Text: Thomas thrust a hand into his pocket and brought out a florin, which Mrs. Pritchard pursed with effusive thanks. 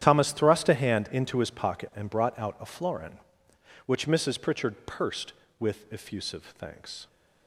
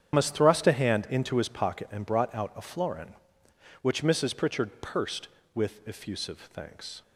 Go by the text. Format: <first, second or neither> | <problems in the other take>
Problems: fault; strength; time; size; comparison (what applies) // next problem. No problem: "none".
first | loses the start of "Thomas"; at 0.1 s; 135 ms // starts louder than the rest; strong; until 1.1 s; 9 dB; strong in the first